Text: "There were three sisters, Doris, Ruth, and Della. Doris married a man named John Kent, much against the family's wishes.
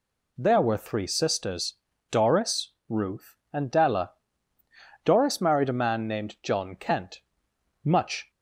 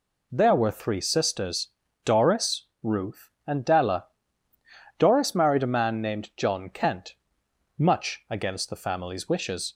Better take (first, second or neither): second